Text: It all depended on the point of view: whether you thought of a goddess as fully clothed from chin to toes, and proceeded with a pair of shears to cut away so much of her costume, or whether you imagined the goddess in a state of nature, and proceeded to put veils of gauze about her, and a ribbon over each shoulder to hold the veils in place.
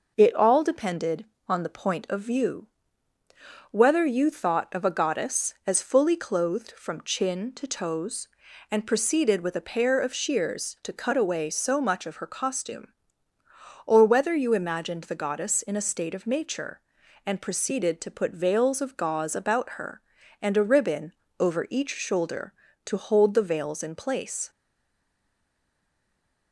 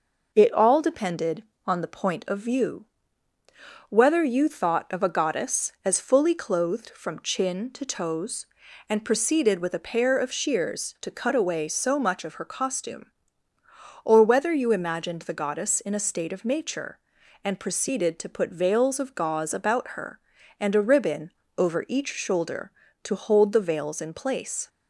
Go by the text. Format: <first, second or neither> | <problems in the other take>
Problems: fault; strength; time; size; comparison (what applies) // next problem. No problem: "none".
second | pauses between "ribbon" and "over"; slight; at 21.1 s; 0.26 s long; slight in the second // stays silent after the last word; noticeable; from 24.5 s on; 2.0 s long